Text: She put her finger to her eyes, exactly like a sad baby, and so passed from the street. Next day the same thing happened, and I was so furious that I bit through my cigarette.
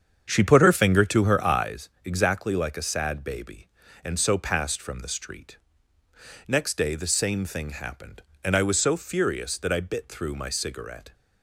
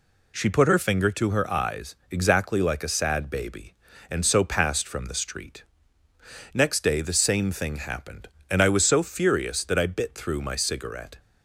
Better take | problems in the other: second | starts louder than the rest; strong; until 1.9 s; 7.5 dB

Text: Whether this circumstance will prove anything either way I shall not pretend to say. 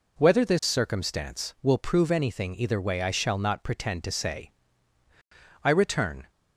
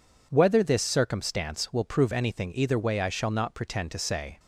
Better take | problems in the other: second | goes on to say "I return"; noticeable; from 5.6 s on; 0.66 s long

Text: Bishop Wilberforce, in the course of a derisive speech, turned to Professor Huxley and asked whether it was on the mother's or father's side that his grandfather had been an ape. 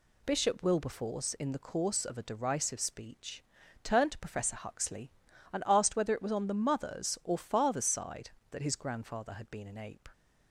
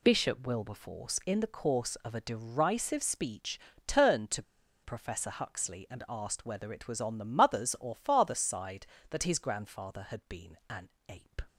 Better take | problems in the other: first | pauses between "to" and "Professor"; at 4.4 s; 0.41 s long // pauses between "an" and "ape"; slight; at 10.8 s; 0.20 s long

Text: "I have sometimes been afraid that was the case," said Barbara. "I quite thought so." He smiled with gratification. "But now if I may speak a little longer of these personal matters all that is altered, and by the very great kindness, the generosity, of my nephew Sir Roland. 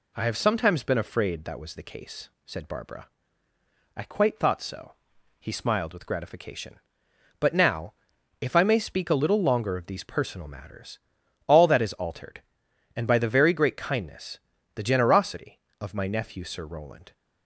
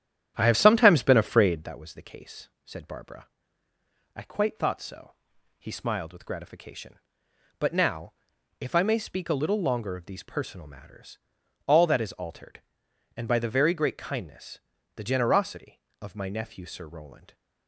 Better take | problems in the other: first | starts louder than the rest; strong; until 1.7 s; 10.5 dB // pauses between "now" and "if"; noticeable; at 8.1 s; 0.48 s long; noticeable in the first // pauses between "matters" and "all"; noticeable; at 11.1 s; 0.48 s long; noticeable in the first

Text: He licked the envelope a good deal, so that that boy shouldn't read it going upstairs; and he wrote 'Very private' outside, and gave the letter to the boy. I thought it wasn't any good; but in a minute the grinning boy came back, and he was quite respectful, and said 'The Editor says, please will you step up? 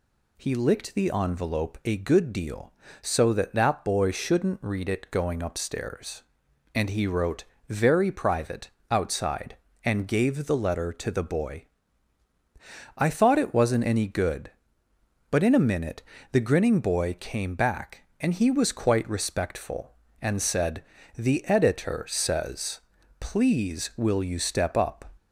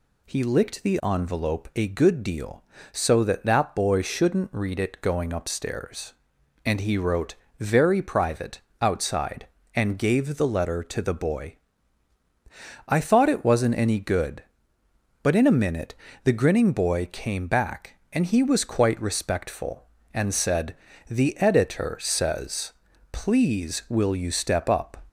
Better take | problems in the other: neither | pauses between "wrote" and "Very"; slight; the same in both // pauses between "private" and "outside"; slight; the same in both // pauses between "minute" and "the"; slight; the same in both // pauses between "said" and "The"; slight; the same in both

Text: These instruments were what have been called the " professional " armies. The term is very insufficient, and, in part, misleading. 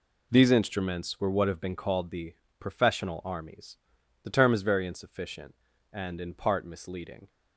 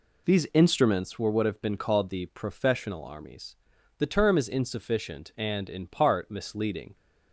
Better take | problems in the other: first | skips "very"; at 4.4 s

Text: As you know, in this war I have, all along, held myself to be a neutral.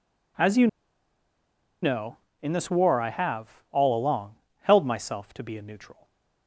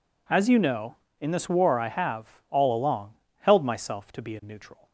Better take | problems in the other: second | pauses between "you" and "know"; at 0.6 s; 1.1 s long // stays silent after the last word; slight; from 5.9 s on; 0.5 s long

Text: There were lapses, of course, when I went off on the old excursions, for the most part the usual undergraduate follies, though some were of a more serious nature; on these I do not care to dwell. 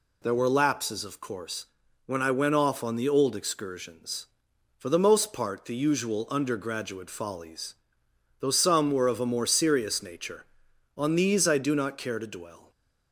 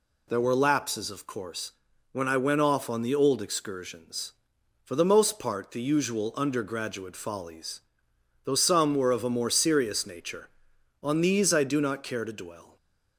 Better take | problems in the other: neither | none

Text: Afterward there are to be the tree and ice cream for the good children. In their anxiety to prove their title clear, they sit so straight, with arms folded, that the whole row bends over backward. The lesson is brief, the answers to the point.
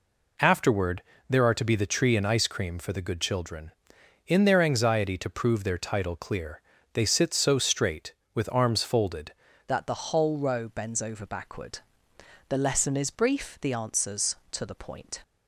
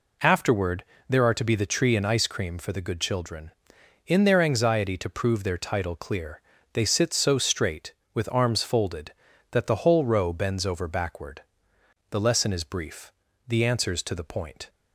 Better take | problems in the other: second | pauses between "Afterward" and "there"; slight; at 1.0 s; 0.28 s long; slight in the second // changes voice at "that"; from 9.6 s on; 5.6 s long

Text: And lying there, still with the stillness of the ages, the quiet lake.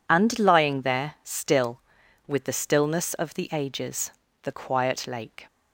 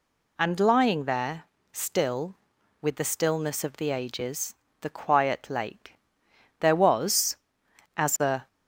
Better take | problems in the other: first | goes on to say "There was as a"; strong; from 6.5 s on; 1.8 s long

